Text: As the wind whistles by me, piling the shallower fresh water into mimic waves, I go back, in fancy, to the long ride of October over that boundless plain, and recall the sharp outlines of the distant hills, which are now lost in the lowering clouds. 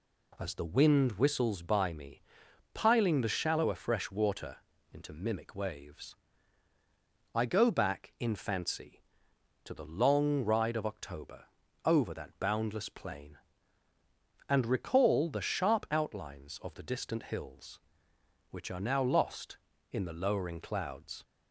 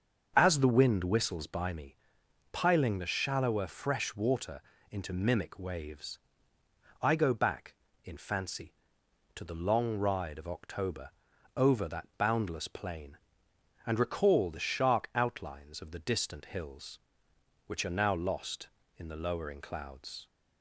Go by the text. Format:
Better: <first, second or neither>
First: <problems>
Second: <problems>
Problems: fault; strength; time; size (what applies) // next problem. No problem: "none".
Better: first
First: pauses between "water" and "into"; slight; at 4.5 s; 0.34 s long // pauses between "October" and "over"; at 11.4 s; 0.40 s long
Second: starts louder than the rest; until 1.3 s; 6.5 dB // pauses between "water" and "into"; slight; at 4.6 s; 0.30 s long // pauses between "October" and "over"; at 11.1 s; 0.44 s long // says "shark" for "sharp"; at 14.5 s